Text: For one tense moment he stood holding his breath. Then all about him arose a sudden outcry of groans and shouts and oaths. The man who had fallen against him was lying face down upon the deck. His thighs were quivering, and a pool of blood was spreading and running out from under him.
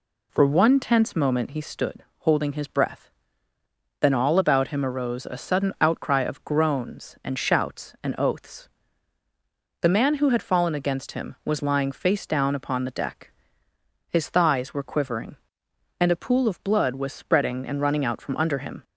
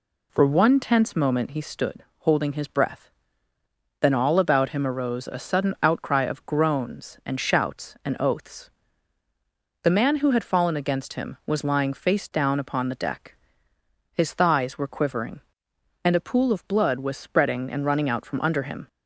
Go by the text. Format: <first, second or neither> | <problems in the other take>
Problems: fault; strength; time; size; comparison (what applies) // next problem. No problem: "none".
neither | pauses between "stood" and "holding"; slight; the same in both